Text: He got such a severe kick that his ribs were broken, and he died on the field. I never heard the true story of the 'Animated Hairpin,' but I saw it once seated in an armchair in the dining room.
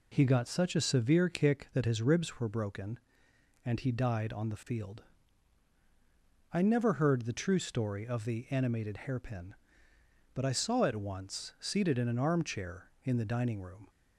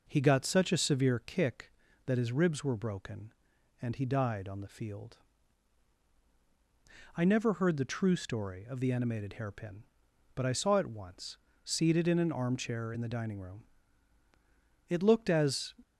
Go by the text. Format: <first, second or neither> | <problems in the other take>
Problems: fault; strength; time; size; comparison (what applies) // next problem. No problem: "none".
first | pauses between "once" and "seated"; slight; at 11.3 s; 0.28 s long // goes on to say "It looked as"; noticeable; from 14.8 s on; 0.84 s long